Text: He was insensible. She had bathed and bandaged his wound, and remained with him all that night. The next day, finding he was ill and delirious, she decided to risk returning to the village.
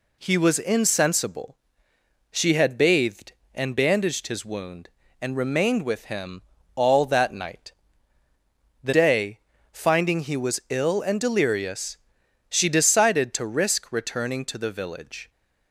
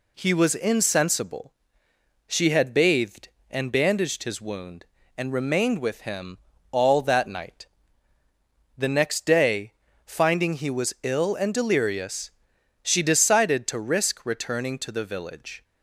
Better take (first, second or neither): second